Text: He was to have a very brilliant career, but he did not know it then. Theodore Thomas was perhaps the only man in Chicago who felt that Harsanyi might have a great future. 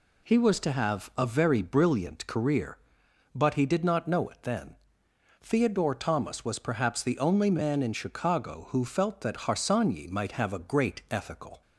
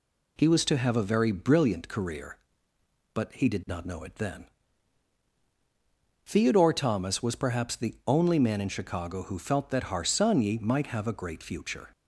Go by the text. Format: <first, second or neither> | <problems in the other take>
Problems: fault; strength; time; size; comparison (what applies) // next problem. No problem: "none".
second | says "ethical" for "future"; at 11.0 s